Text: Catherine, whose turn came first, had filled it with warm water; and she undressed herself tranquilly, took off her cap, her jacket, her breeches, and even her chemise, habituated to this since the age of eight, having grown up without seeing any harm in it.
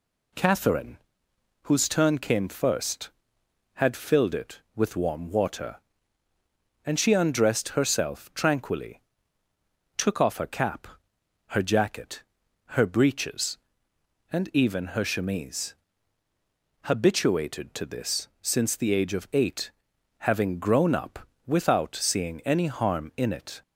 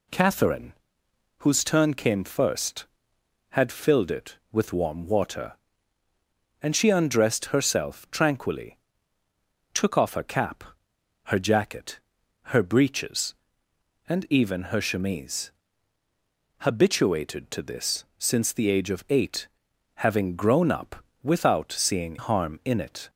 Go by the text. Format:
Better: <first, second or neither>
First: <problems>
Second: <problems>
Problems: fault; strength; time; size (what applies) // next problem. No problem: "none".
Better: first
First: pauses between "up" and "without"; slight; at 21.2 s; 0.18 s long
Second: pauses between "up" and "without"; slight; at 21.0 s; 0.18 s long // skips "any"; at 22.1 s